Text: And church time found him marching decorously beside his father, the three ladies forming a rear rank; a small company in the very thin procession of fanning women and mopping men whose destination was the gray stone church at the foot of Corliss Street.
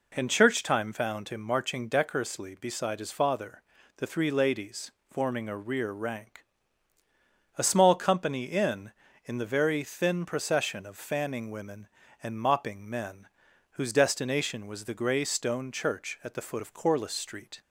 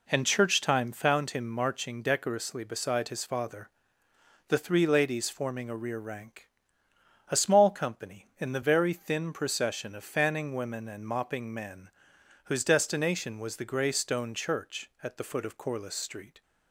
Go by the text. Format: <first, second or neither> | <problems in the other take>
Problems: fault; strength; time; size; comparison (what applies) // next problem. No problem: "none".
second | pauses between "ladies" and "forming"; slight; at 4.9 s; 0.20 s long // says "in" twice; at 9.2 s // pauses between "men" and "whose"; noticeable; at 13.2 s; 0.50 s long; noticeable in the second